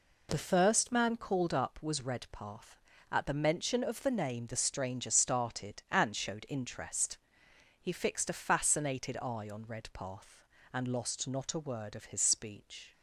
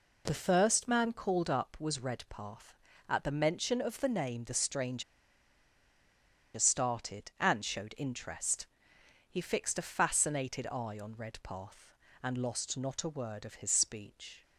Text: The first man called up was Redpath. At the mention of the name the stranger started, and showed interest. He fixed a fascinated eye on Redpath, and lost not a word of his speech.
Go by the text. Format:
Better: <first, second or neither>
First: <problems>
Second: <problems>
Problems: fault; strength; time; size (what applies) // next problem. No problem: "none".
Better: first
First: none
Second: pauses between "stranger" and "started"; strong; at 5.0 s; 1.5 s long